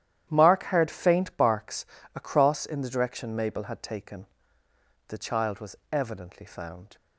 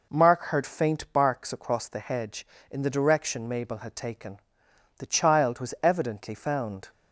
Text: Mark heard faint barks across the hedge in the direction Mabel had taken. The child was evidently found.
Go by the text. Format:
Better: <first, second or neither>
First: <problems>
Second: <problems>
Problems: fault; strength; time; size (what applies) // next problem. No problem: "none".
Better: second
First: starts louder than the rest; strong; until 1.3 s; 11.5 dB // pauses between "barks" and "across"; slight; at 1.8 s; 0.28 s long // skips "the hedge"; at 2.6 s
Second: none